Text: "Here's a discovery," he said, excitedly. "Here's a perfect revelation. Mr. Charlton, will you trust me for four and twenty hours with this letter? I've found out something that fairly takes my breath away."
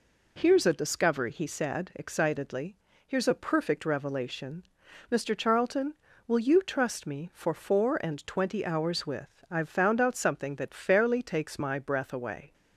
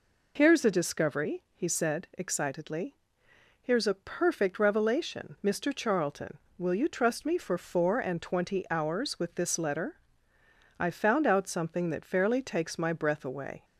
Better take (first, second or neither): second